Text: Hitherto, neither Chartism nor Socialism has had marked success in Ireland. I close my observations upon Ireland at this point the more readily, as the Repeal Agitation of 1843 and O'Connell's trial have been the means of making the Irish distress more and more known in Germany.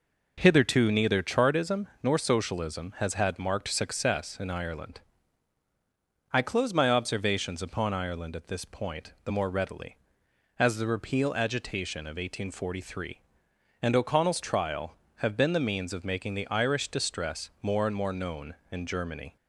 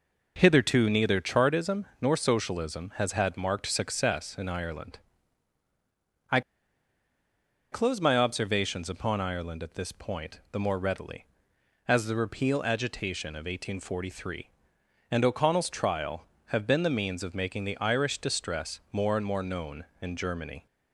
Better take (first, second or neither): first